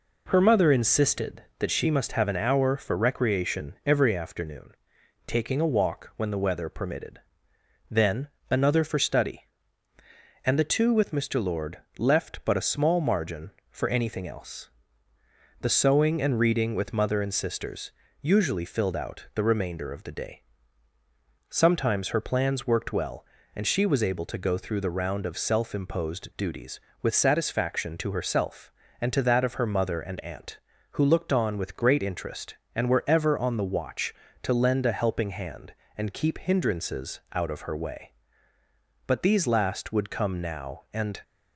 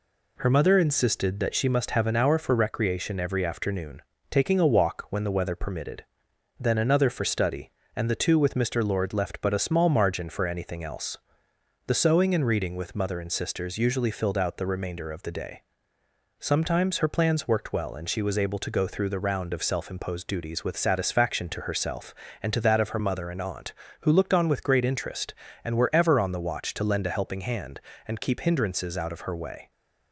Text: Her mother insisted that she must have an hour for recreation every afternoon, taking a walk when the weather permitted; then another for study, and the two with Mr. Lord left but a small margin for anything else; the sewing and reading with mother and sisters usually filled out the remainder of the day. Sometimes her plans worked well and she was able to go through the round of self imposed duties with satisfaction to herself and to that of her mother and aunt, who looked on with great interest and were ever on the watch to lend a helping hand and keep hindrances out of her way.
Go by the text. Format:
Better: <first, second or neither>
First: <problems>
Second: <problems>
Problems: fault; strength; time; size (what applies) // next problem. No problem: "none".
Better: second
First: pauses between "then" and "another"; slight; at 8.2 s; 0.22 s long // pauses between "Lord" and "left"; slight; at 11.7 s; 0.20 s long // pauses between "sisters" and "usually"; slight; at 17.9 s; 0.30 s long // goes on to say "But these last would come now and"; strong; from 39.0 s on; 2.1 s long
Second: none